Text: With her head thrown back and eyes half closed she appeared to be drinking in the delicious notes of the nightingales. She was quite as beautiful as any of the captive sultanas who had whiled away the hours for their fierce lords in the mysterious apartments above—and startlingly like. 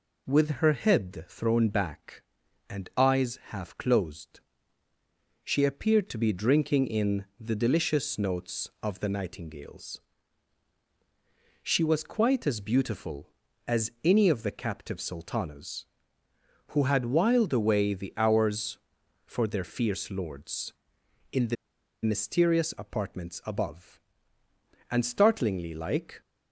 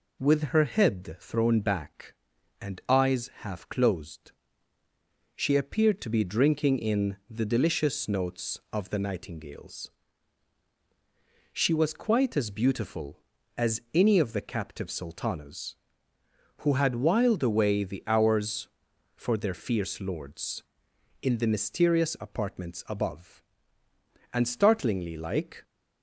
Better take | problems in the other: second | pauses between "closed" and "she"; at 4.3 s; 1.0 s long; also in the second // pauses between "the" and "mysterious"; noticeable; at 21.5 s; 0.49 s long

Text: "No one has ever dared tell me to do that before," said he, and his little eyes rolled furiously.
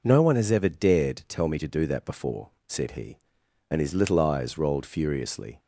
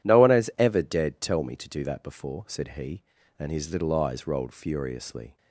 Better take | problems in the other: neither | none

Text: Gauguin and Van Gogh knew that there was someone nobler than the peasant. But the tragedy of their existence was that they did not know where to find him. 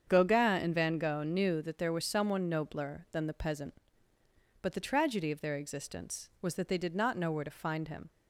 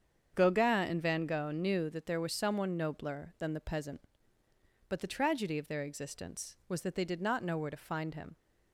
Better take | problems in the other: neither | starts louder than the rest; strong; the same in both

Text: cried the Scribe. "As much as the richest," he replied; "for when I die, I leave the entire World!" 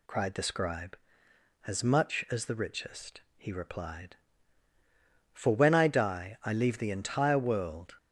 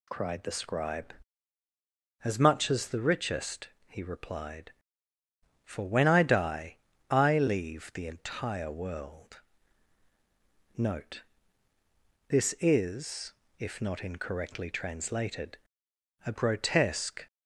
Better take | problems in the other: first | goes on to say "Note This is if not incorrectly translated a grotesque"; strong; from 10.7 s on; 6.5 s long

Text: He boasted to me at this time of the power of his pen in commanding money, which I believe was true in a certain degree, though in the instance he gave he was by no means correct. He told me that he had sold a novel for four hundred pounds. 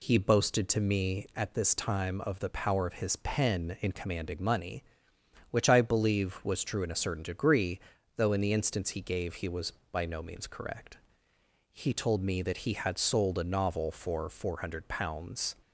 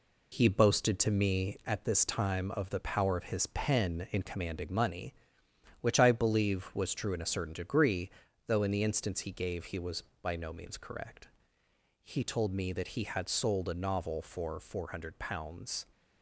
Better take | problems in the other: first | gets quieter; noticeable; throughout; 6 dB

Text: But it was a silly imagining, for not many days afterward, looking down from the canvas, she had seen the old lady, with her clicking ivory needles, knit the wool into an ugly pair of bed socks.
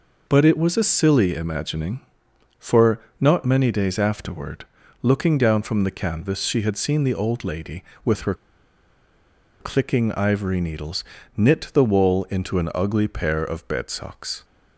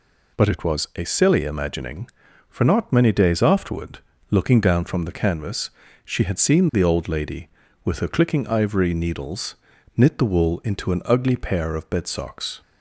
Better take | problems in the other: second | pauses between "for" and "not"; slight; at 2.9 s; 0.22 s long // pauses between "her" and "clicking"; strong; at 8.3 s; 1.2 s long

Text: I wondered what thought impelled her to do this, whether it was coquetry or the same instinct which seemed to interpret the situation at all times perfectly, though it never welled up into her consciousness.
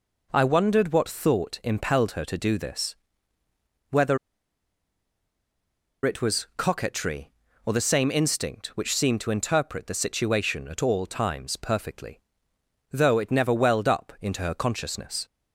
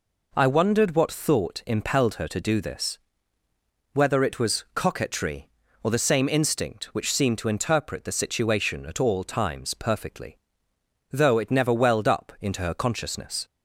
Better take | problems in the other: second | pauses between "whether" and "it"; strong; at 4.1 s; 1.8 s long

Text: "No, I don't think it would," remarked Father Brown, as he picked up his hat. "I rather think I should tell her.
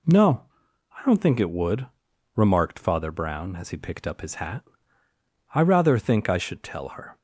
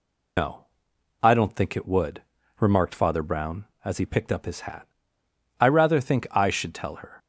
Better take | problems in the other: first | loses the start of "No"; at 0.3 s; 155 ms

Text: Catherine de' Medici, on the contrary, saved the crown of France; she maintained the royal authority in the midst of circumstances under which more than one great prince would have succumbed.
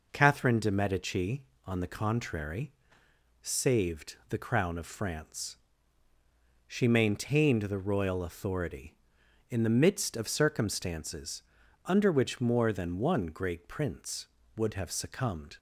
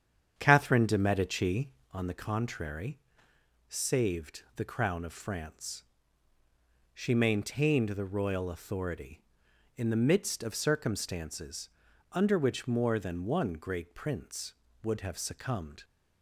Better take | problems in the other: first | starts louder than the rest; strong; until 2.0 s; 8 dB // pauses between "circumstances" and "under"; at 11.7 s; 0.42 s long; also in the first

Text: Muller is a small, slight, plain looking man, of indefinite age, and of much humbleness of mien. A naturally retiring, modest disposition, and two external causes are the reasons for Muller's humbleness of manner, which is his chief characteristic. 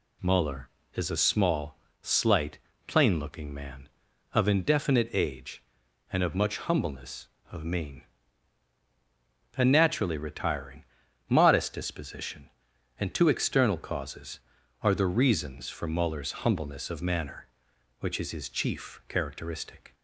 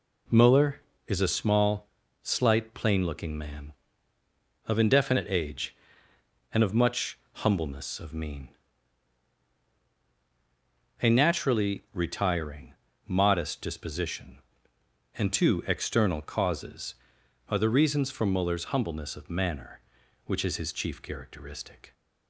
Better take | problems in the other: neither | none

